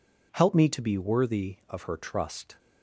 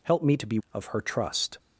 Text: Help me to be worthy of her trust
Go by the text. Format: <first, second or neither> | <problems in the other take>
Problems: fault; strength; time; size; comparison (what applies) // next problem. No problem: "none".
first | skips "worthy"; at 0.6 s